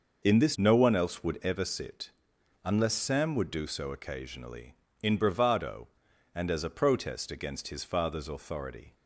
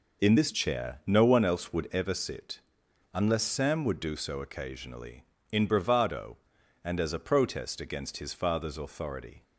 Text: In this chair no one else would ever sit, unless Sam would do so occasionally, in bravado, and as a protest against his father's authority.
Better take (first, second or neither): second